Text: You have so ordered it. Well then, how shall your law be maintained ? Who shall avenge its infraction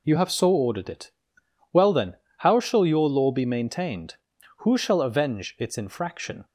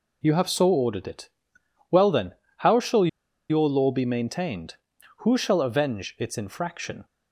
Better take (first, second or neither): first